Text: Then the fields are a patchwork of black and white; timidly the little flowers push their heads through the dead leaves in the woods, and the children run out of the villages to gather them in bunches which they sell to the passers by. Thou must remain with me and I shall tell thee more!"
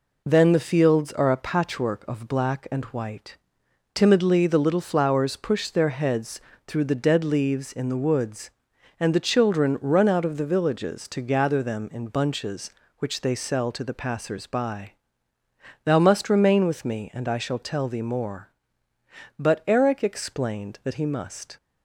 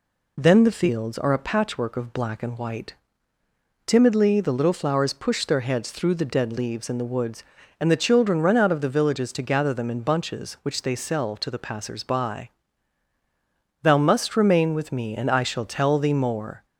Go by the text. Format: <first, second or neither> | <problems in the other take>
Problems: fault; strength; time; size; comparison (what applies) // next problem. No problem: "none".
second | pauses between "heads" and "through"; slight; at 6.4 s; 0.26 s long // goes on to say "But Eric explained that he must"; strong; from 19.3 s on; 2.1 s long